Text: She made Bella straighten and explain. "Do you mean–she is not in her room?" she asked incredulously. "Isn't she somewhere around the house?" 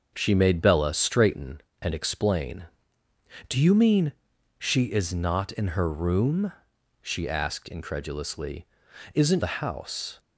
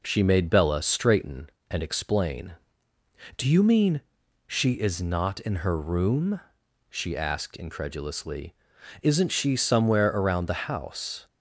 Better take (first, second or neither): second